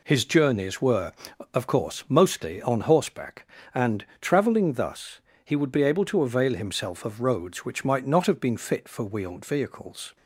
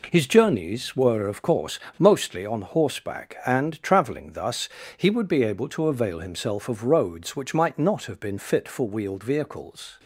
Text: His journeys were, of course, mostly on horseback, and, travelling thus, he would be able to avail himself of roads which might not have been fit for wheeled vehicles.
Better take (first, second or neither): neither